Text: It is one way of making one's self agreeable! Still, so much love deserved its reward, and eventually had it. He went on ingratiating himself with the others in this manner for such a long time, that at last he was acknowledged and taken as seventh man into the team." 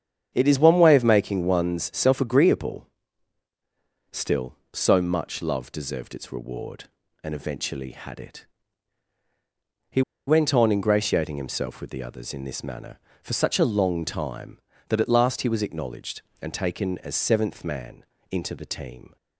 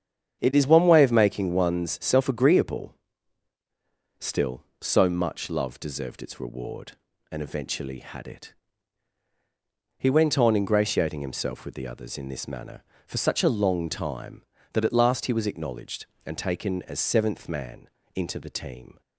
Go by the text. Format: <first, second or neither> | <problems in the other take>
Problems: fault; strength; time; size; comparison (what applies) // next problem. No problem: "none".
second | starts louder than the rest; strong; until 1.3 s; 8 dB; strong in the second // pauses between "He" and "went"; slight; at 10.0 s; 0.26 s long // pauses between "man" and "into"; slight; at 18.0 s; 0.26 s long; slight in the second